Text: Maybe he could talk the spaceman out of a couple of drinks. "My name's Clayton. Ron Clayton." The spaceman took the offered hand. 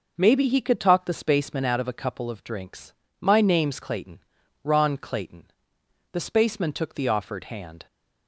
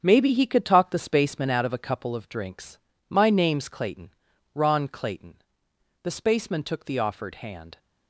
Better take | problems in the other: first | gets quieter; strong; throughout; 9 dB

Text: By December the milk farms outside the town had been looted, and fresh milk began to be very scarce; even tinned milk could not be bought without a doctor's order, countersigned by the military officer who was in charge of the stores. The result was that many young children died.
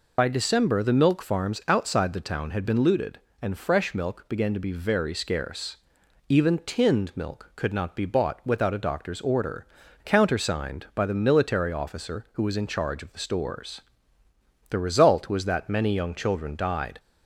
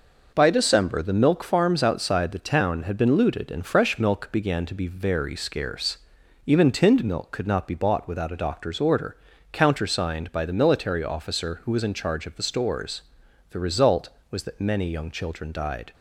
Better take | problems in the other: second | loses the start of "By"; at 0.1 s; 50 ms

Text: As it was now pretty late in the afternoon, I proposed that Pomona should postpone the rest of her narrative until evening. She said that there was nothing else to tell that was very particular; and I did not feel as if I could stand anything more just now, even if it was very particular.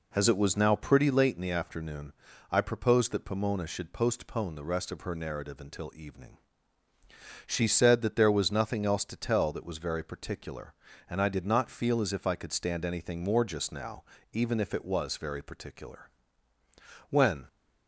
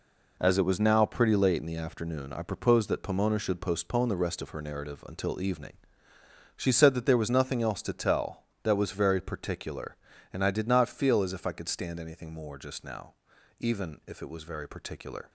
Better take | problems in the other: second | goes on to say "When"; slight; from 17.0 s on; 0.38 s long

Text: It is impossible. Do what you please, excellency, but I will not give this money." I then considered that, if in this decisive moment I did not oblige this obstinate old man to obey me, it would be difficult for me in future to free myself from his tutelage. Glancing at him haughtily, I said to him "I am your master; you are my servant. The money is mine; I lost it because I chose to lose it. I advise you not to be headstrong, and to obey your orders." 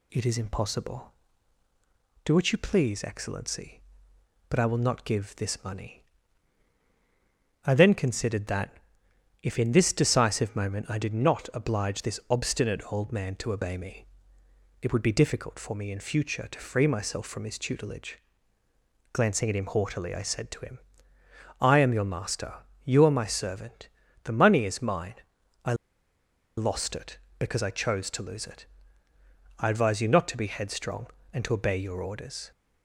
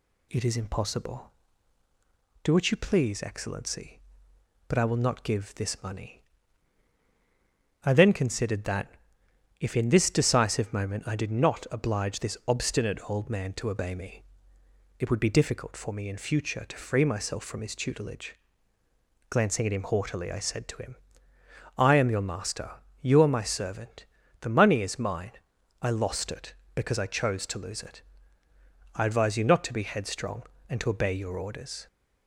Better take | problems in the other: second | pauses between "him" and "I"; noticeable; at 20.7 s; 0.82 s long; noticeable in the second // pauses between "I" and "lost"; noticeable; at 25.7 s; 0.83 s long

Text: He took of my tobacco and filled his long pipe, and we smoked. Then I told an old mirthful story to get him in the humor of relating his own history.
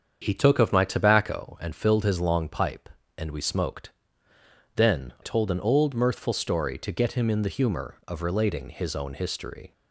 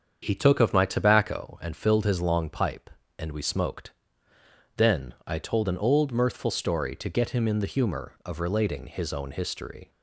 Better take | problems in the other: second | starts louder than the rest; strong; until 1.2 s; 7.5 dB; strong in the second // skips "I"; at 5.1 s

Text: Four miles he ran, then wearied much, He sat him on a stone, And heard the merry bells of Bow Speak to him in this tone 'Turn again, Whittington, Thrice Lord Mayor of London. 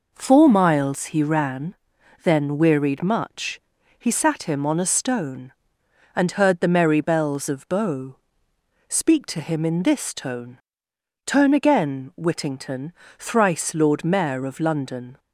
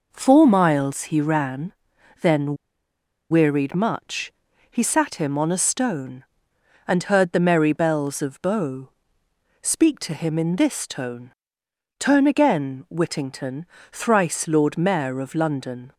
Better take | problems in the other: first | pauses between "then" and "wearied"; noticeable; at 2.5 s; 0.76 s long // pauses between "Bow" and "Speak"; noticeable; at 8.8 s; 0.72 s long; noticeable in the first // pauses between "tone" and "Turn"; noticeable; at 11.3 s; 0.66 s long; noticeable in the first

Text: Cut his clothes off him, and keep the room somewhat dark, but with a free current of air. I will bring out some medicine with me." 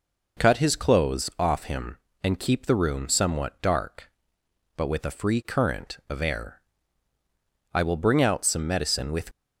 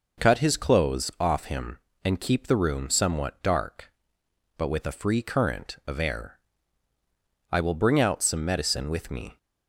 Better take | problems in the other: second | stops before "me"; at 9.3 s

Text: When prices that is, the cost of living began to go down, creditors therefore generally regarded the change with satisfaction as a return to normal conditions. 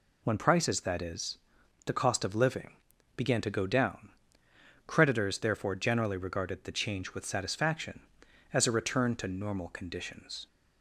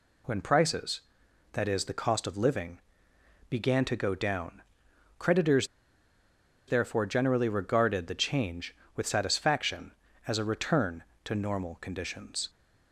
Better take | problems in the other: first | pauses between "living" and "began"; noticeable; at 2.7 s; 0.70 s long; also in the first // pauses between "creditors" and "therefore"; at 5.6 s; 1.0 s long

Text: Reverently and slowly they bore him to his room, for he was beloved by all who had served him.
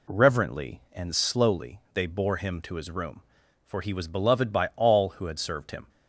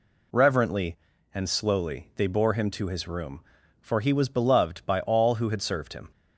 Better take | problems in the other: neither | none

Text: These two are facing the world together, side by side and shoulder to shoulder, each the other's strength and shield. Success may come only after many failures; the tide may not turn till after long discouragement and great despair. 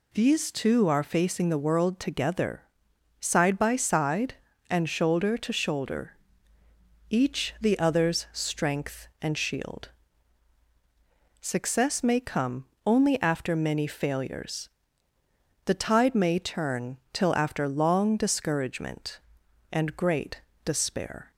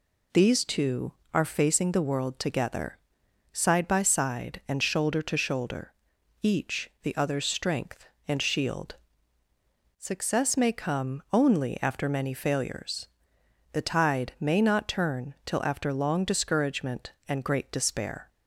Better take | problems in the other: second | pauses between "come" and "only"; slight; at 12.6 s; 0.20 s long // skips "not"; at 16.4 s // pauses between "turn" and "till"; slight; at 16.9 s; 0.16 s long // pauses between "great" and "despair"; slight; at 20.4 s; 0.24 s long

